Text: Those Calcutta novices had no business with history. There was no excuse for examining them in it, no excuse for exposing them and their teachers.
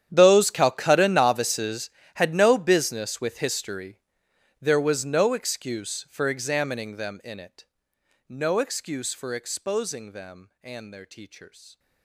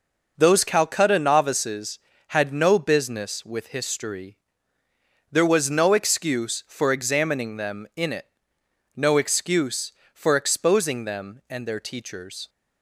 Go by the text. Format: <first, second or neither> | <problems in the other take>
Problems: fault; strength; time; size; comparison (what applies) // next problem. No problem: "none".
second | gets quieter; strong; throughout; 21 dB